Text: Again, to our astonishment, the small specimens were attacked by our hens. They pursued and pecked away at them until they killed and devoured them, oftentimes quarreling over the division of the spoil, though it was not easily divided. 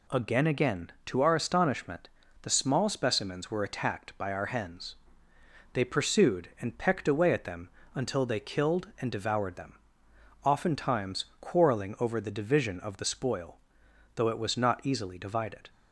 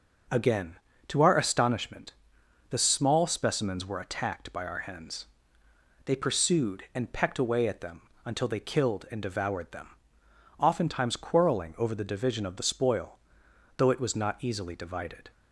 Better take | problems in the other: second | says "Again" twice; at 0.4 s // pauses between "them" and "until"; slight; at 7.6 s; 0.24 s long; slight in the second // pauses between "oftentimes" and "quarreling"; slight; at 11.2 s; 0.16 s long

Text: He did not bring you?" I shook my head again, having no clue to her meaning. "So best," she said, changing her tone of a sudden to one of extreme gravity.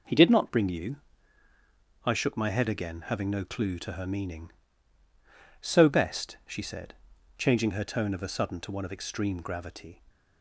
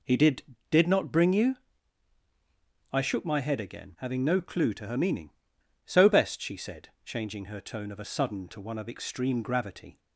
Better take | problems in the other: first | says "did" twice; at 0.6 s

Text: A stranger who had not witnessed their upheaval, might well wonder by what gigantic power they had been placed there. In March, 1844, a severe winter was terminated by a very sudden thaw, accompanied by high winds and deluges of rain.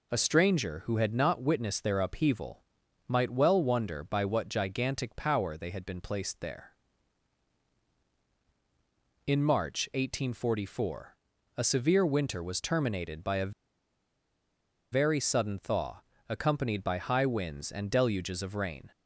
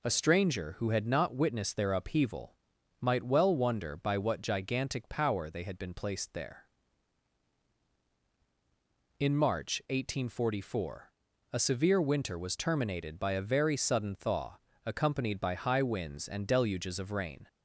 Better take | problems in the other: second | pauses between "a" and "very"; strong; at 13.5 s; 1.4 s long

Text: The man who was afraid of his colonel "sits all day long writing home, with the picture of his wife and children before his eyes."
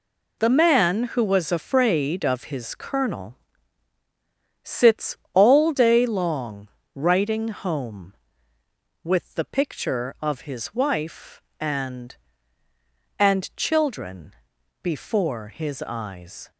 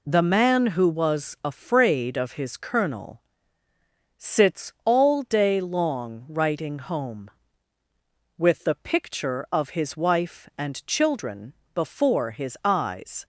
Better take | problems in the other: second | pauses between "colonel" and "sits"; strong; at 3.3 s; 1.2 s long; noticeable in the second // pauses between "sits" and "all"; slight; at 5.1 s; 0.18 s long // pauses between "long" and "writing"; slight; at 6.6 s; 0.26 s long // says "and" twice; at 13.1 s // pauses between "children" and "before"; noticeable; at 14.3 s; 0.52 s long; slight in the second

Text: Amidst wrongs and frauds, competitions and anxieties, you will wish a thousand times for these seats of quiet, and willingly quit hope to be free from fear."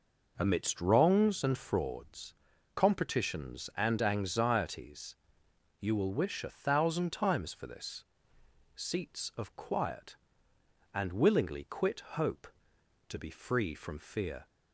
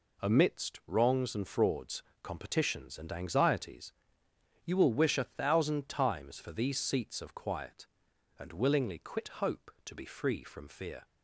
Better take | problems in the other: second | says "this" for "these"; at 7.6 s

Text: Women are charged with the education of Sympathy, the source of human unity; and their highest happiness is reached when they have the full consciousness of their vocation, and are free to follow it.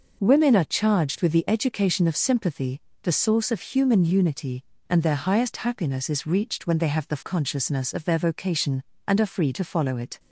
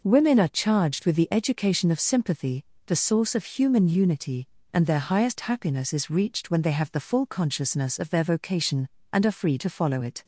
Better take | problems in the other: second | skips "full"; at 7.2 s

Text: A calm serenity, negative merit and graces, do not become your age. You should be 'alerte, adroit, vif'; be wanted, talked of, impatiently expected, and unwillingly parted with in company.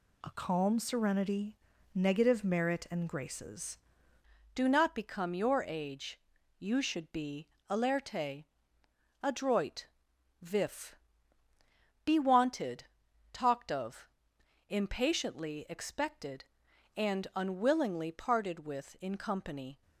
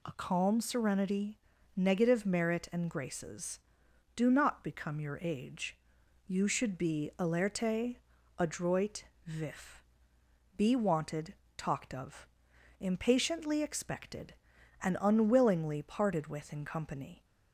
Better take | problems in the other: second | changes voice at "do"; from 4.5 s on; 15.3 s long // pauses between "be" and "alerte"; slight; at 7.4 s; 0.20 s long

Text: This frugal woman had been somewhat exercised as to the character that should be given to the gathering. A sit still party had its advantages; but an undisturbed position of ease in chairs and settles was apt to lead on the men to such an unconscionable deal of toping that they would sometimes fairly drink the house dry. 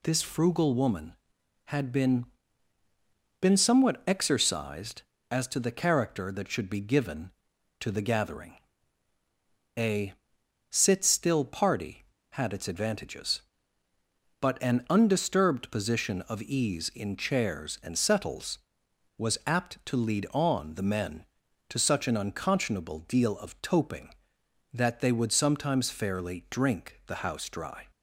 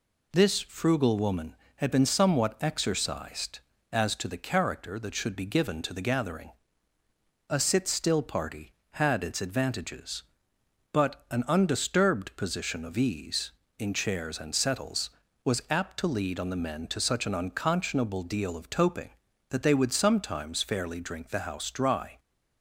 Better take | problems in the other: second | says "been" twice; at 3.4 s // pauses between "A" and "sit"; noticeable; at 10.1 s; 0.58 s long

